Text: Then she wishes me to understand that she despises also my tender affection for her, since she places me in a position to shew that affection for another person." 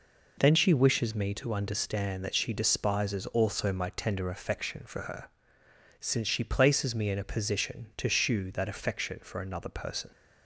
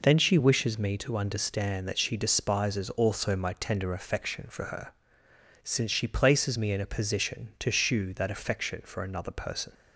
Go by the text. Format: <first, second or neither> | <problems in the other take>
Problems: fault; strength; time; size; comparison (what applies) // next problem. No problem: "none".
neither | none